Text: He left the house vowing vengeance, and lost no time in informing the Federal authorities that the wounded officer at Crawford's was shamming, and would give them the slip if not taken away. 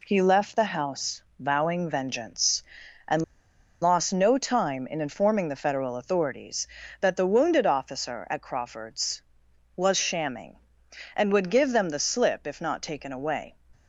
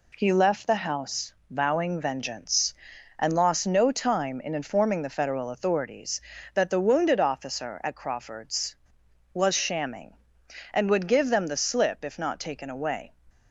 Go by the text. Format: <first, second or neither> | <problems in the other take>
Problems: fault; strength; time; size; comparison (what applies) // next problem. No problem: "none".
second | pauses between "house" and "vowing"; slight; at 1.2 s; 0.16 s long; slight in the second // pauses between "and" and "lost"; noticeable; at 3.2 s; 0.59 s long